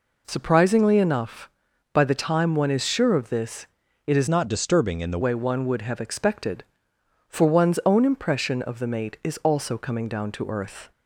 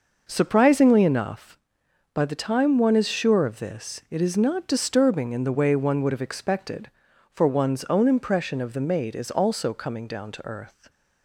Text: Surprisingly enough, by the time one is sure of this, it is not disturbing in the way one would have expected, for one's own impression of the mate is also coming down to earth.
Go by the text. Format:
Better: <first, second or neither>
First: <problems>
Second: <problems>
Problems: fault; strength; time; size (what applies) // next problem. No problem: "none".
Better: second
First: changes voice from "not" to "the"; from 4.2 to 5.1 s; 0.9 s long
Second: none